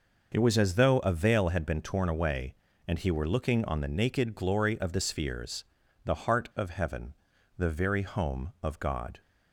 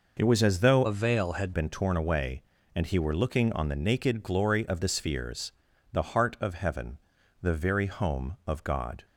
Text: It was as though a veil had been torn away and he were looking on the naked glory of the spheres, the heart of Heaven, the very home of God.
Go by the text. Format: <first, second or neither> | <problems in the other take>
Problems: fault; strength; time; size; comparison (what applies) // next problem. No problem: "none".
first | changes voice from "a" to "had"; from 0.8 to 1.5 s; 0.7 s long